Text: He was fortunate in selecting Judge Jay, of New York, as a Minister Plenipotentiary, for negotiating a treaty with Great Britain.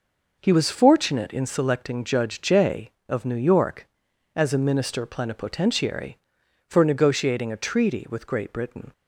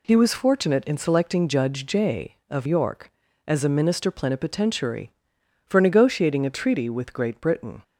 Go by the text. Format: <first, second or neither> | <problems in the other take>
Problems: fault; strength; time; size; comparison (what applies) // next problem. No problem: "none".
first | skips "New"; at 2.6 s